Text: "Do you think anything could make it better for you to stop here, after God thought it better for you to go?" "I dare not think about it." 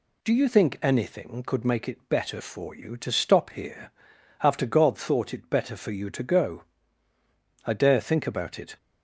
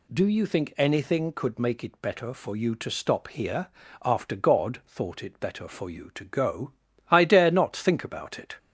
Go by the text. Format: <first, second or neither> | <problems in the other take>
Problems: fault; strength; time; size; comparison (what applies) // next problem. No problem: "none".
second | skips "not"; at 8.0 s